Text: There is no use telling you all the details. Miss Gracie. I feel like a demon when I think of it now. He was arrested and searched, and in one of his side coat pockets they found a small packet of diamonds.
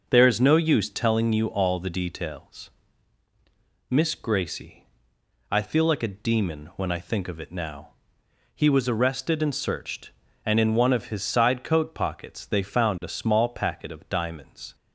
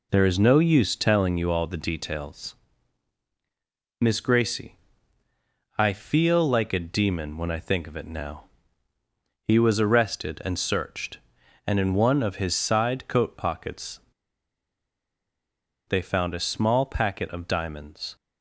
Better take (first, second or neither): first